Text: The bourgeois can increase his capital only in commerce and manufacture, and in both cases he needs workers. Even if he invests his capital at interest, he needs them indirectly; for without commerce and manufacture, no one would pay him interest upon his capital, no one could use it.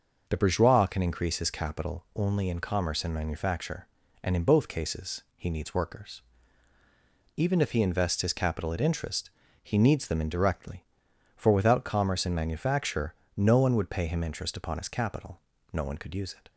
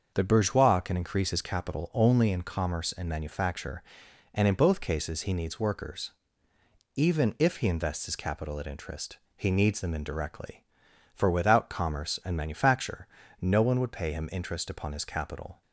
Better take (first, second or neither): first